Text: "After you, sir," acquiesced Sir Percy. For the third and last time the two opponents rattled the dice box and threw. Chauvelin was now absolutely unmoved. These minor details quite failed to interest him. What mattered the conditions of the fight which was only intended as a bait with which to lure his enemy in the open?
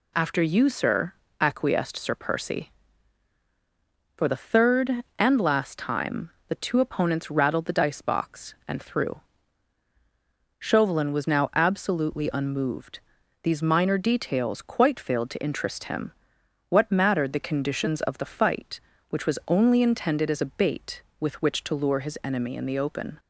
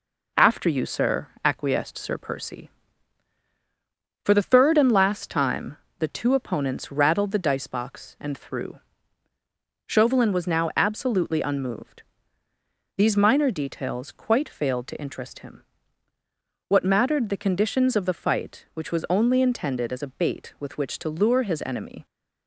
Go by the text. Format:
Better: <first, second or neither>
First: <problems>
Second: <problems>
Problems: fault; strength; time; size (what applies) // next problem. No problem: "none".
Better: first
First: pauses between "time" and "the"; slight; at 6.2 s; 0.20 s long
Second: pauses between "time" and "the"; slight; at 5.7 s; 0.22 s long // stops before "in the open"; at 22.0 s